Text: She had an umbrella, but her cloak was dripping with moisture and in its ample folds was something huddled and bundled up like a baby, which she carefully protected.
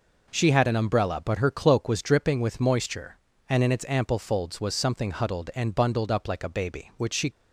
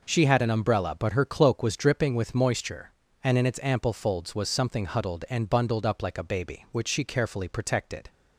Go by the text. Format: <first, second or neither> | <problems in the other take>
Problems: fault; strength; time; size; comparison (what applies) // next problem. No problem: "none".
second | stops before "carefully protected"; at 7.3 s